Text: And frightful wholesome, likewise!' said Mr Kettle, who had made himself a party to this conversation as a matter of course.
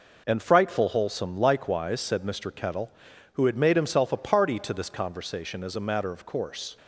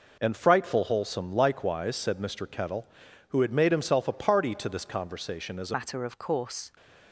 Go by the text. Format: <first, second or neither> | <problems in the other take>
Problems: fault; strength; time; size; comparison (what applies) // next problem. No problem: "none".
first | changes voice at "matter"; from 5.7 s on; 0.9 s long